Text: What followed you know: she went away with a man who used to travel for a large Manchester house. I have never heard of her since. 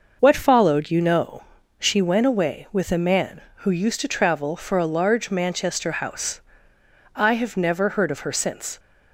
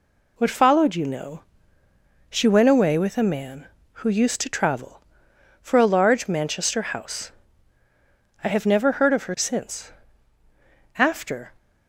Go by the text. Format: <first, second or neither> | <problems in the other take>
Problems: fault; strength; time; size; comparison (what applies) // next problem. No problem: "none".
first | goes on to say "After"; from 10.9 s on; 0.56 s long